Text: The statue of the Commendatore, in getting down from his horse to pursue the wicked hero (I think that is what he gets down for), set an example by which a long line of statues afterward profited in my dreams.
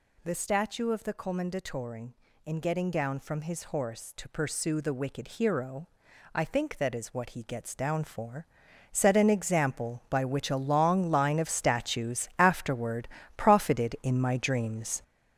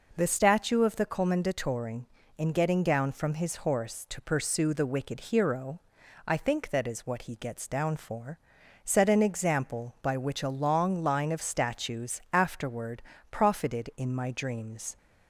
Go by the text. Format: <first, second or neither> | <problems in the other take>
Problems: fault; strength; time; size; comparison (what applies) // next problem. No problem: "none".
second | gets louder; throughout; 6.5 dB // pauses between "afterward" and "profited"; slight; at 13.0 s; 0.28 s long; slight in the second